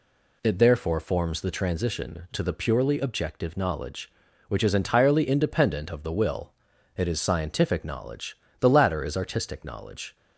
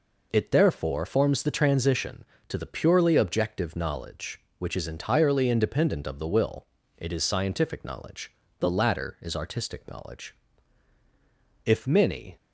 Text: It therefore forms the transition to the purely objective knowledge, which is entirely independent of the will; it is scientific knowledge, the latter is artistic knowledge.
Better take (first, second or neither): first